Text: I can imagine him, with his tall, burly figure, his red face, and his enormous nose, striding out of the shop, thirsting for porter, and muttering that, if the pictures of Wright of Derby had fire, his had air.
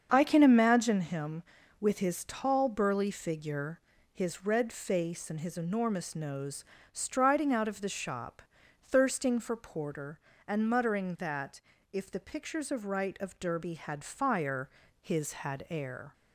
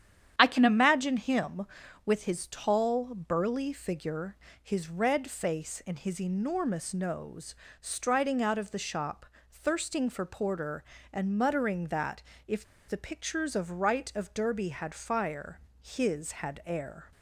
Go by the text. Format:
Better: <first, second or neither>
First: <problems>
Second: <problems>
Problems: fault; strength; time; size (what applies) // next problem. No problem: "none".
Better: first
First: starts louder than the rest; until 1.1 s; 7 dB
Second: starts louder than the rest; strong; until 1.3 s; 9.5 dB // pauses between "if" and "the"; slight; at 12.6 s; 0.23 s long